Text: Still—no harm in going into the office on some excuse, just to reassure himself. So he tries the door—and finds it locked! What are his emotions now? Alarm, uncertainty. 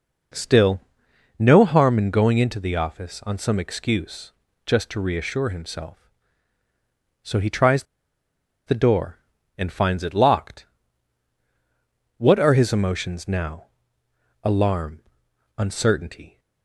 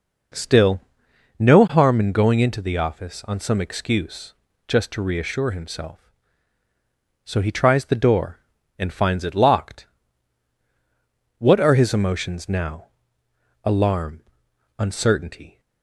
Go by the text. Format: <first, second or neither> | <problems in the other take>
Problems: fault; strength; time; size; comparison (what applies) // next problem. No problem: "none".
second | pauses between "tries" and "the"; noticeable; at 7.8 s; 0.83 s long